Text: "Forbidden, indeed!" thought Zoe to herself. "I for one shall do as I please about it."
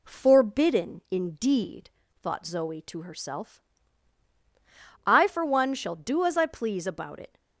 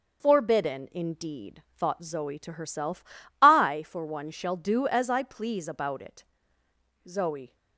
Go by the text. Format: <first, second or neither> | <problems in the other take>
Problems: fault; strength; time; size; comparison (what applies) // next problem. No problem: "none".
first | starts louder than the rest; until 1.2 s; 6 dB // goes on to say "Zoe"; slight; from 7.0 s on; 0.48 s long